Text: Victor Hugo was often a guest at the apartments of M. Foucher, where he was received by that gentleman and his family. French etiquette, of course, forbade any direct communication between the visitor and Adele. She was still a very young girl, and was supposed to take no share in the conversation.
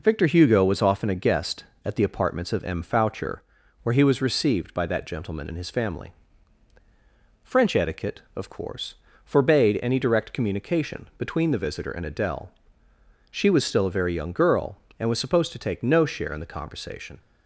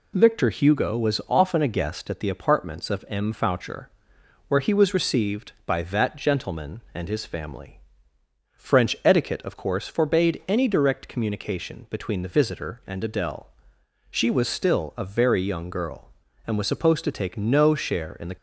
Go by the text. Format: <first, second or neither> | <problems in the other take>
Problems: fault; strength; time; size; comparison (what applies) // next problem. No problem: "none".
first | stops before "conversation"; at 18.3 s